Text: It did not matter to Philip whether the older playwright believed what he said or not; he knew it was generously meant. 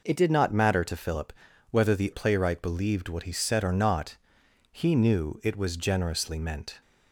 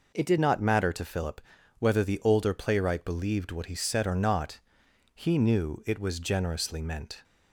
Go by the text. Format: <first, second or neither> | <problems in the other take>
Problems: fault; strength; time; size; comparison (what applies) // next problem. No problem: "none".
second | pauses between "Philip" and "whether"; at 1.3 s; 0.40 s long; also in the second // skips "older"; at 2.1 s